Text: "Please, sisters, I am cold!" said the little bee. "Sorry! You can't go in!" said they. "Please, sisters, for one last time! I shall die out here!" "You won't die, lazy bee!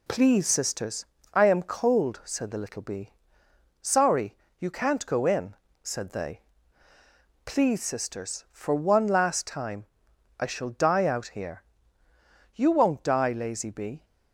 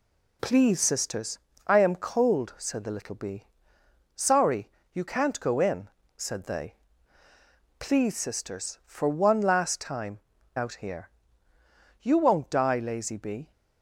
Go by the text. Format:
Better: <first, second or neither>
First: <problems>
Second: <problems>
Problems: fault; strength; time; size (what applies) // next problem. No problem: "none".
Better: first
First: none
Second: skips "I shall die"; at 10.3 s